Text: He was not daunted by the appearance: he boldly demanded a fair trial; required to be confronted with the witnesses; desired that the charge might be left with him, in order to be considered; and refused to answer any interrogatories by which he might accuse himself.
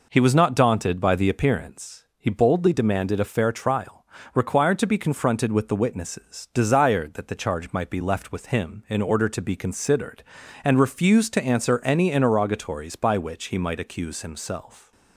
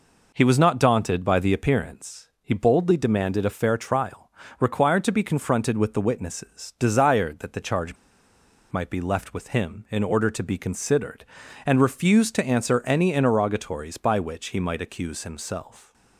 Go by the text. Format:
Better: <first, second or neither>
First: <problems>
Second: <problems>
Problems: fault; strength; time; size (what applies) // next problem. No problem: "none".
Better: first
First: none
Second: pauses between "charge" and "might"; noticeable; at 7.9 s; 0.76 s long